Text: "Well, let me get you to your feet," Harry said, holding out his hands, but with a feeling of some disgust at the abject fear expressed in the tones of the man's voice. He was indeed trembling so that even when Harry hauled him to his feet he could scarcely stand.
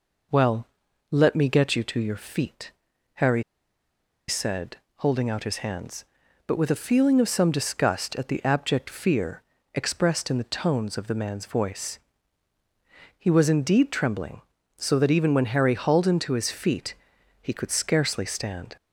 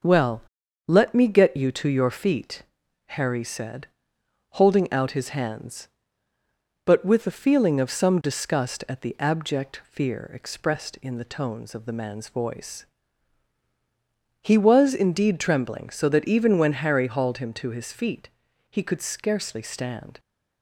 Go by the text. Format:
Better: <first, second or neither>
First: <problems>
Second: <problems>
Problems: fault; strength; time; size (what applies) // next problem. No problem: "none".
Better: second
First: pauses between "Harry" and "said"; noticeable; at 3.4 s; 0.85 s long // pauses between "fear" and "expressed"; slight; at 9.4 s; 0.34 s long // pauses between "feet" and "he"; at 16.9 s; 0.44 s long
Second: pauses between "feet" and "he"; at 18.2 s; 0.40 s long